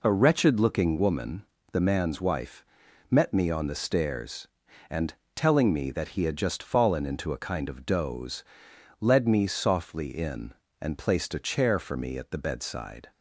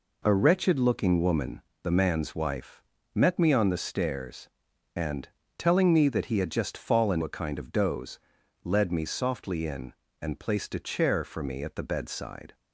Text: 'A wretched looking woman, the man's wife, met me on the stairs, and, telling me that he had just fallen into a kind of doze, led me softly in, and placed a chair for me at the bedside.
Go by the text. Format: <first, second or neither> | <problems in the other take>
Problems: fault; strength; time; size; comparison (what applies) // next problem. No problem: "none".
first | skips "into"; at 7.2 s